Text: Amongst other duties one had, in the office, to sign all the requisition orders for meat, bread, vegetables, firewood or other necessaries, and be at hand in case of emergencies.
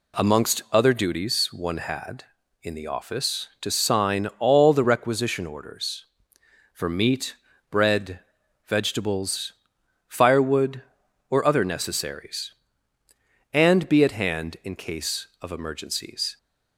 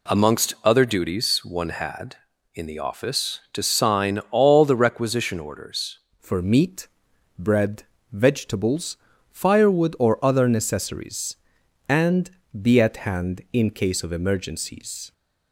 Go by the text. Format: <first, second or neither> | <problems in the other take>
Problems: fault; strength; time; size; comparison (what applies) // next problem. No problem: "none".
first | changes voice at "for"; from 6.2 s on; 8.9 s long // pauses between "and" and "be"; slight; at 12.2 s; 0.32 s long